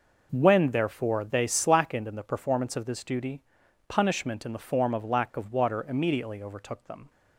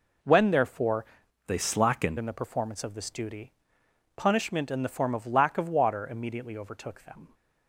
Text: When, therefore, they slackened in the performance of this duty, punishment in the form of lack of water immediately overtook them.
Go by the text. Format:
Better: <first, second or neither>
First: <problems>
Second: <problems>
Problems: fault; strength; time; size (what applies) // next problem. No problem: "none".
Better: first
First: none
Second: changes voice from "they" to "slackened"; from 1.4 to 2.1 s; 0.7 s long